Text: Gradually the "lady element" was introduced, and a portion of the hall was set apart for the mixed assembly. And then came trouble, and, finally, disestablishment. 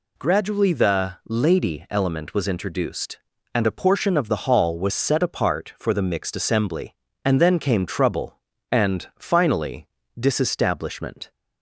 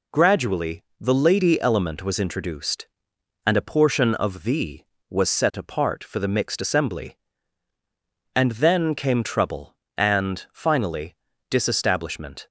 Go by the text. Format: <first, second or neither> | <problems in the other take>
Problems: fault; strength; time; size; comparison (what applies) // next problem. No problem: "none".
first | pauses between "Gradually" and "the"; slight; at 0.8 s; 0.16 s long // skips "hall"; at 4.9 s